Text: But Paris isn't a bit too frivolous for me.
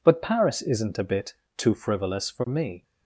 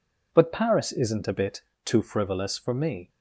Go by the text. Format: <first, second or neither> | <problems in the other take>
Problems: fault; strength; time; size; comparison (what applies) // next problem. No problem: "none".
neither | pauses between "bit" and "too"; slight; the same in both